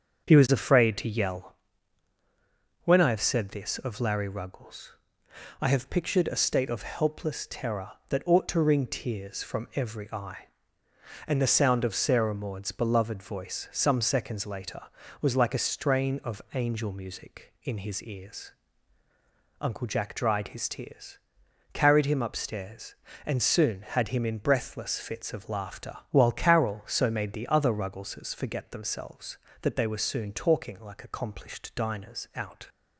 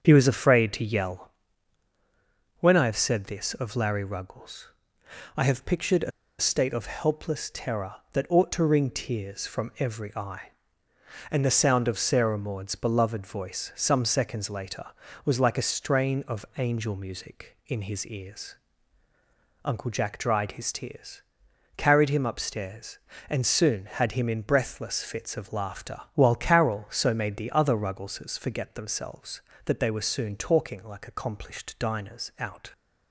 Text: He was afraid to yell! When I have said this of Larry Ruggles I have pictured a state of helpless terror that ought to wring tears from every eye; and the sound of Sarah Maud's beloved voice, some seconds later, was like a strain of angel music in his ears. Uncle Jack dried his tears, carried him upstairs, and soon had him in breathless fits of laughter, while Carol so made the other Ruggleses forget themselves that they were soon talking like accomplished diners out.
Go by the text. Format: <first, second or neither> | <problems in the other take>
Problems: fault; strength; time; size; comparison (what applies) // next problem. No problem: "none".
first | starts louder than the rest; strong; until 1.0 s; 7 dB; also in the first // pauses between "Ruggles" and "I"; noticeable; at 4.6 s; 0.68 s long; noticeable in the first // pauses between "a" and "state"; slight; at 6.1 s; 0.28 s long